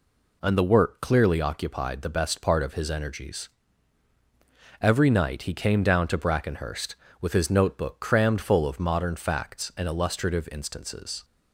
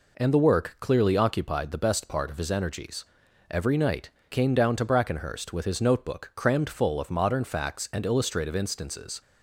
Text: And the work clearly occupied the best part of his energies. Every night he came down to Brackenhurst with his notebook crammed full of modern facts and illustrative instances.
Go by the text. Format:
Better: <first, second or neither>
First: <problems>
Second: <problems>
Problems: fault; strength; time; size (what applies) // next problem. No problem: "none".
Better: first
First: none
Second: skips "he"; at 4.2 s